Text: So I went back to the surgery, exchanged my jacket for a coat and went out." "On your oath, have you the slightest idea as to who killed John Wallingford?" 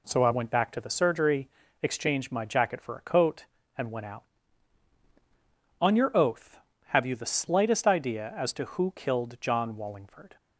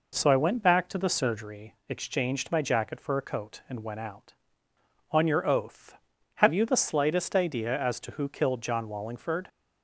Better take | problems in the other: neither | none

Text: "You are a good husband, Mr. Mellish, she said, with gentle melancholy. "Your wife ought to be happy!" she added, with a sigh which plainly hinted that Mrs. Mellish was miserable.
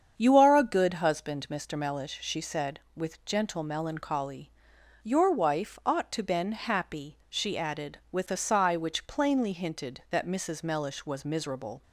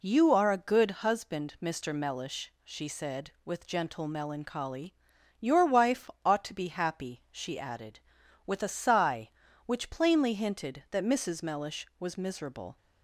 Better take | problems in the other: second | starts louder than the rest; strong; until 1.2 s; 7.5 dB // says "been" for "be"; at 6.2 s

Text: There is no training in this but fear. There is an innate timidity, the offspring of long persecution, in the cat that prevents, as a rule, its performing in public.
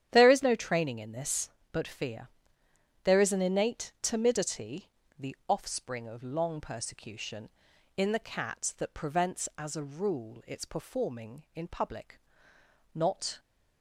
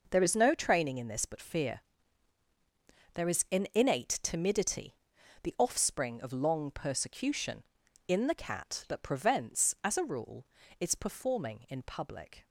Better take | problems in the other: second | starts louder than the rest; strong; until 1.1 s; 10 dB // goes on to say "Not"; slight; from 12.9 s on; 0.44 s long

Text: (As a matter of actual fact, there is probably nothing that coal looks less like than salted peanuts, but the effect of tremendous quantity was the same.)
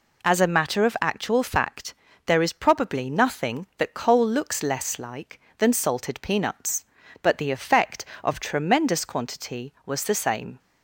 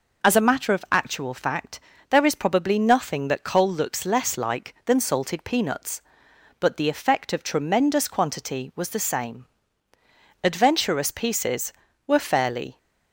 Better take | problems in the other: first | goes on to say "Adventurous pieces were fairly"; strong; from 10.4 s on; 2.3 s long

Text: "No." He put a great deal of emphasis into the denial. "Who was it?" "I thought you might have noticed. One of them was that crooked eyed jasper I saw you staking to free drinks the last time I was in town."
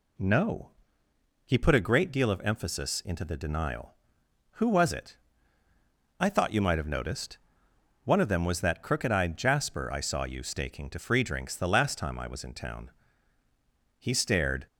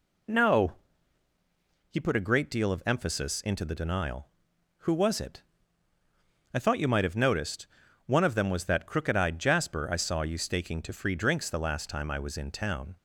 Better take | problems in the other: second | goes on to say "He stared"; noticeable; from 13.9 s on; 0.68 s long

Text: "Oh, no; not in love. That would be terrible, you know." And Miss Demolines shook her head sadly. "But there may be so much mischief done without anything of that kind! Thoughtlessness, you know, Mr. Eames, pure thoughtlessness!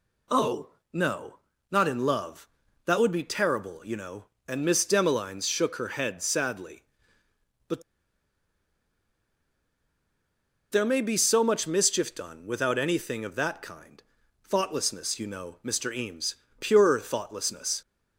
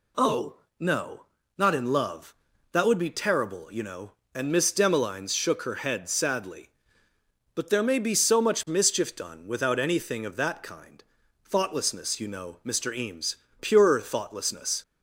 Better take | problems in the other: second | pauses between "But" and "there"; strong; at 7.8 s; 2.8 s long

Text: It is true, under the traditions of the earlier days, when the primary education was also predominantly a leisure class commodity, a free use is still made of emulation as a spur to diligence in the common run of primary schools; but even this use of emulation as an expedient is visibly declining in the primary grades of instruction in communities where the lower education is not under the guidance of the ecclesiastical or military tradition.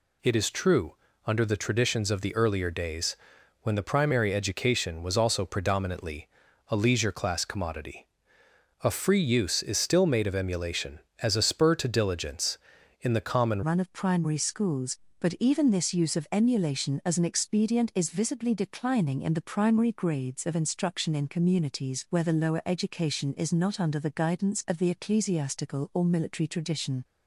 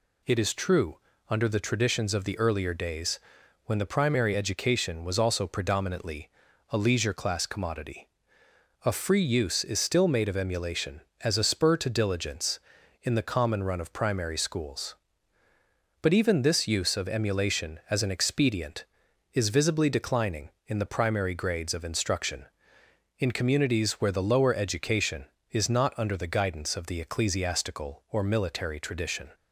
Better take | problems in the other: second | pauses between "predominantly" and "a"; at 6.2 s; 0.40 s long; also in the second // changes voice at "run"; from 13.6 s on; 13.4 s long

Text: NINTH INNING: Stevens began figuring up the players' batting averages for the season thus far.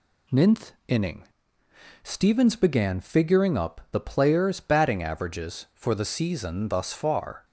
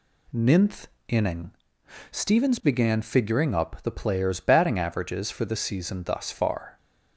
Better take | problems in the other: neither | pauses between "NINTH" and "INNING"; slight; the same in both

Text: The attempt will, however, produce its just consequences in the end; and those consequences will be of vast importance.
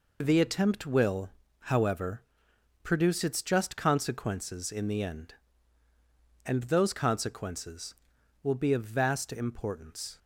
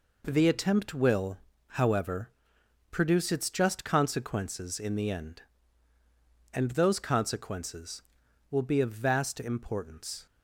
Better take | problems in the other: second | loses the start of "The"; at 0.2 s; 35 ms

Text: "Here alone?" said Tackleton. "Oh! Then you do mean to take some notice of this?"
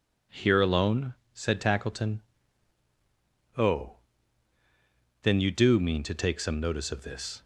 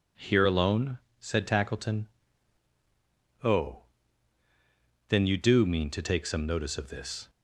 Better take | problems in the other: neither | none

